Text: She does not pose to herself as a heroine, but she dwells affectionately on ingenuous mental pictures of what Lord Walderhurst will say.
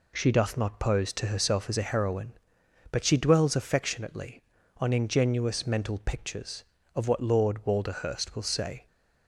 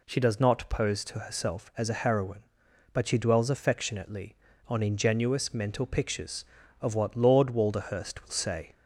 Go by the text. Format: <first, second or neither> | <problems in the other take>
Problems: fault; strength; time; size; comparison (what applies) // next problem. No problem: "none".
second | says "doth" for "does"; at 0.3 s